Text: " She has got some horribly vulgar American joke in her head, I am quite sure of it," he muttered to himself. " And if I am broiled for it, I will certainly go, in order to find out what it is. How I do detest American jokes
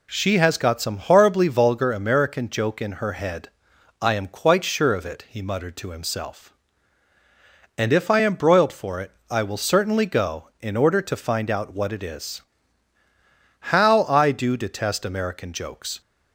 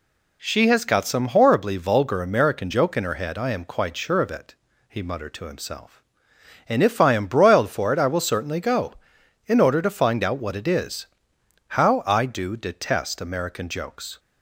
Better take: neither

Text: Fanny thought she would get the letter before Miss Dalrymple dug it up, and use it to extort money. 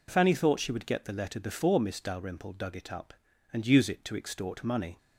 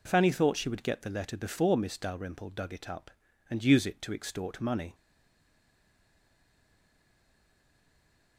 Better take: first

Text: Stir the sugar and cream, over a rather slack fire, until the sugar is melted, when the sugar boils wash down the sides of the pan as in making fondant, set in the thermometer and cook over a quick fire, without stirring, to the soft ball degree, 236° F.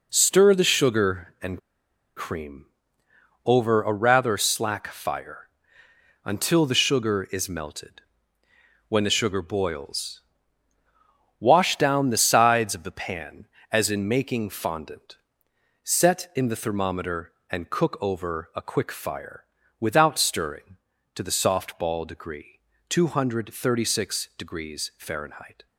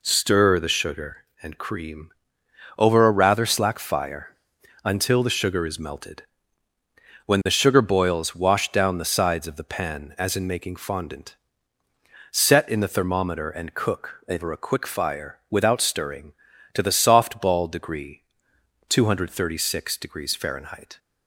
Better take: second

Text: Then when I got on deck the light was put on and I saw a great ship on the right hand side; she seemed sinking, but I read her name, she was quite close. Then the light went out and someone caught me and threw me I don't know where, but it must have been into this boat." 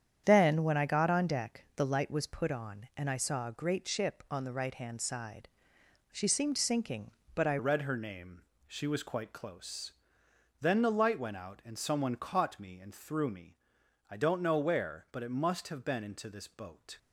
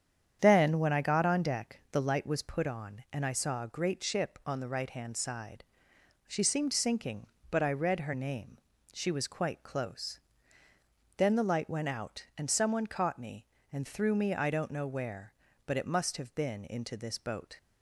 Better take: second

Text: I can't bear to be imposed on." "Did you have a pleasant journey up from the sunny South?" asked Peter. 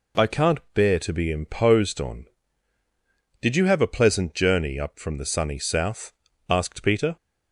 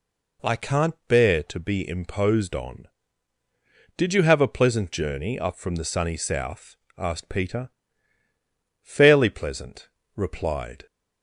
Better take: first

